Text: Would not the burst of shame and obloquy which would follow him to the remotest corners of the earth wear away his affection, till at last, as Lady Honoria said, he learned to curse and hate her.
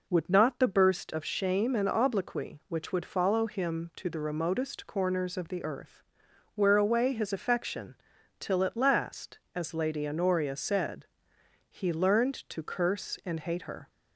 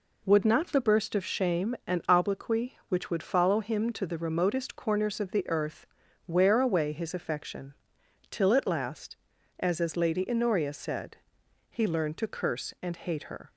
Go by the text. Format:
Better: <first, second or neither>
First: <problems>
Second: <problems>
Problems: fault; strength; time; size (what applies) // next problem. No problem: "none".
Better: first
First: pauses between "earth" and "wear"; noticeable; at 6.0 s; 0.54 s long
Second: pauses between "earth" and "wear"; at 5.8 s; 0.44 s long // says "as" twice; at 9.8 s